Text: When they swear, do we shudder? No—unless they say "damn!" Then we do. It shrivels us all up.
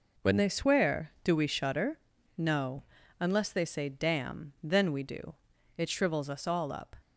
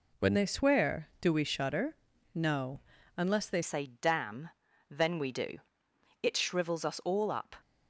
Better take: first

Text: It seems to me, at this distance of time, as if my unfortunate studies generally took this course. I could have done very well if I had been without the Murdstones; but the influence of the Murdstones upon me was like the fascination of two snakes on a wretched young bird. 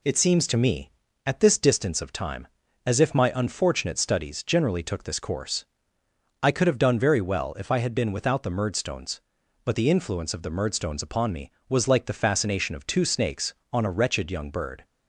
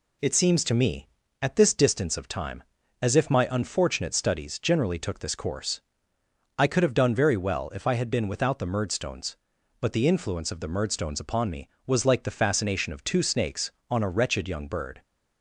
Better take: neither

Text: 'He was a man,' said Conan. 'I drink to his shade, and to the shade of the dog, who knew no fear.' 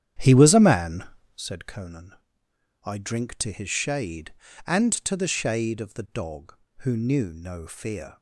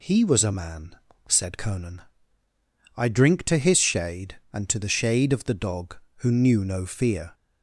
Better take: second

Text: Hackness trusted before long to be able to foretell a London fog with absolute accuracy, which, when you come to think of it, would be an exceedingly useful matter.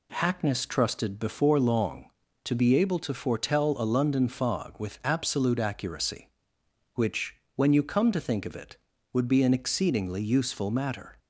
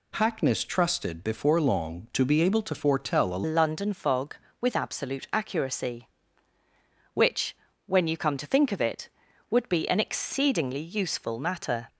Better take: first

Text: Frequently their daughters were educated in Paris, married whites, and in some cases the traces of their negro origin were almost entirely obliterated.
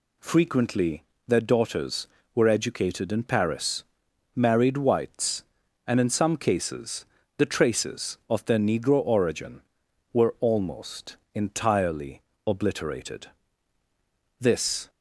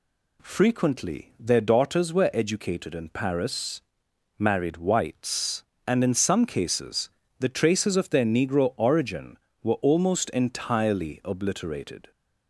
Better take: second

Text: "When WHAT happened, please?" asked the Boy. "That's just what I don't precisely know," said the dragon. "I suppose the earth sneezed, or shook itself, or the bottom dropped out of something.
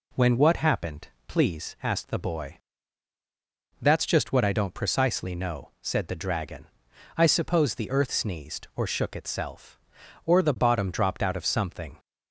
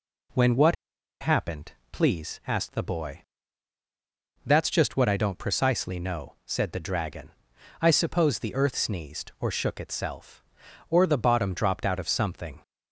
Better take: first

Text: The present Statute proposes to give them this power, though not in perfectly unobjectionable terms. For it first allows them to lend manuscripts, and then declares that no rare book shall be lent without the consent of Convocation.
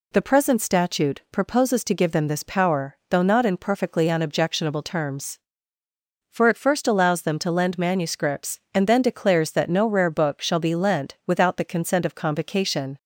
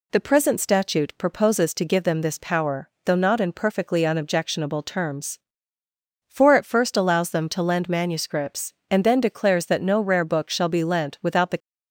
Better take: first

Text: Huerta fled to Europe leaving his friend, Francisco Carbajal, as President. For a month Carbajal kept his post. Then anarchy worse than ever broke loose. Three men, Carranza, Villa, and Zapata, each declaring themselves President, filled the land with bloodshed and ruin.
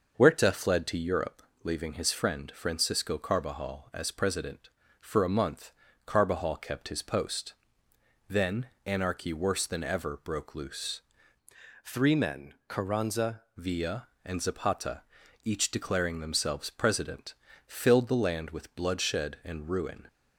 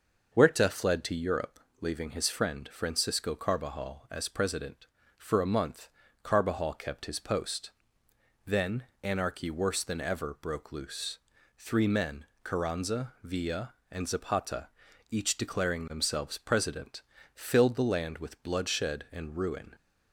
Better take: second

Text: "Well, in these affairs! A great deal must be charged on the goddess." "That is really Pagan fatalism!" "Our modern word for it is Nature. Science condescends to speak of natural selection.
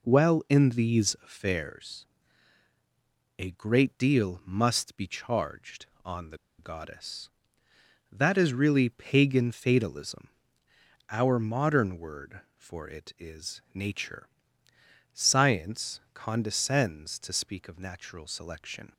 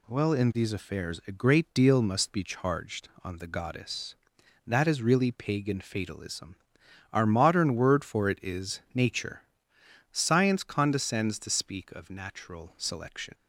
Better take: second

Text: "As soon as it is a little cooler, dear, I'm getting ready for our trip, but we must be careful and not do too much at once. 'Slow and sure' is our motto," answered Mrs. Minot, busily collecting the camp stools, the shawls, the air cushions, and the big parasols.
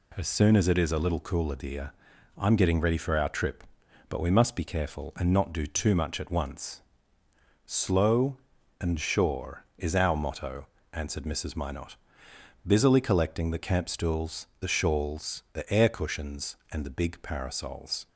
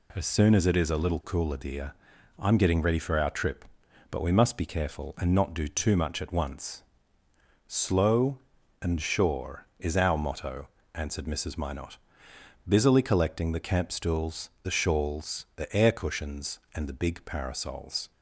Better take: neither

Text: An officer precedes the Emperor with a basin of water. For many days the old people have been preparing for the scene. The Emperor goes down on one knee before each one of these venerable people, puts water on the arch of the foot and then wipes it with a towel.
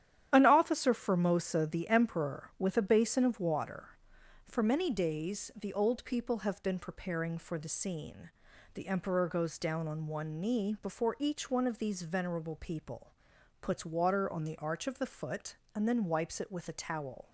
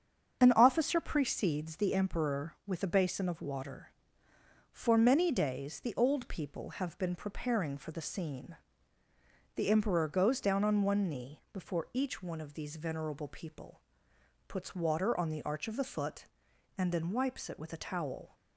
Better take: second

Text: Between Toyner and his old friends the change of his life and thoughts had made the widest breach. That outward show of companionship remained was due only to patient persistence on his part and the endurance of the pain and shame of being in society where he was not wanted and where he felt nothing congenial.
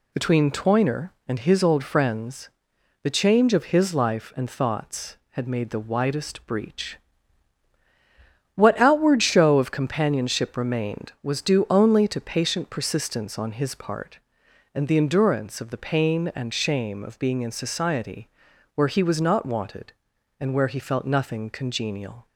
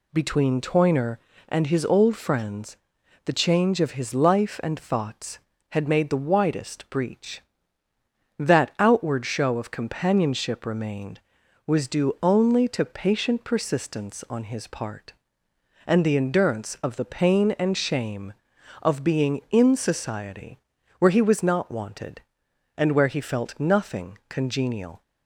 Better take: second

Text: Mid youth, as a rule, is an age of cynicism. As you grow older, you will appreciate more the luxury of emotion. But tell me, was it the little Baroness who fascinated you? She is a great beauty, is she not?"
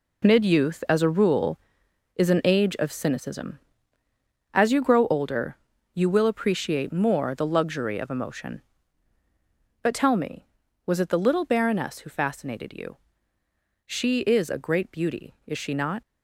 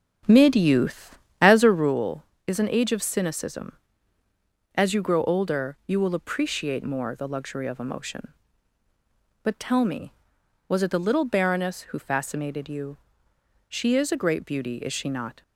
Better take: first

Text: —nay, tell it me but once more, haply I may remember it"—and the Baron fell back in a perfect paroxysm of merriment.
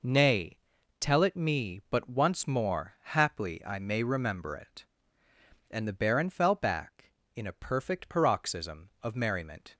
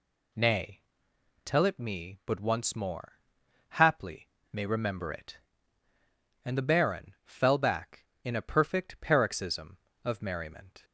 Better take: first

